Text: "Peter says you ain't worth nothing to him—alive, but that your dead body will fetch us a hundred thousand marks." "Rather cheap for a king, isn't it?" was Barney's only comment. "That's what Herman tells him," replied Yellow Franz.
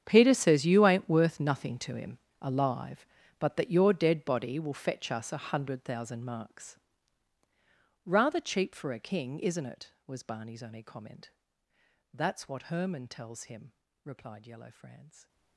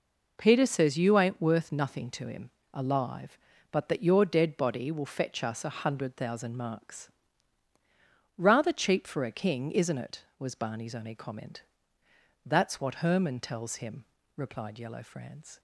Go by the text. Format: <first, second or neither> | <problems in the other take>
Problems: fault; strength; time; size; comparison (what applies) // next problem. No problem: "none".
second | gets quieter; strong; throughout; 18.5 dB